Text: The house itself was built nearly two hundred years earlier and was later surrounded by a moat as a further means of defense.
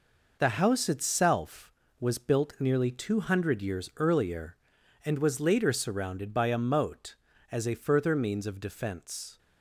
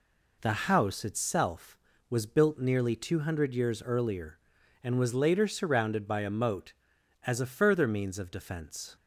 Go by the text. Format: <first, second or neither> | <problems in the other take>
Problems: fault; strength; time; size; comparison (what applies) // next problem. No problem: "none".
second | gets quieter; throughout; 6.5 dB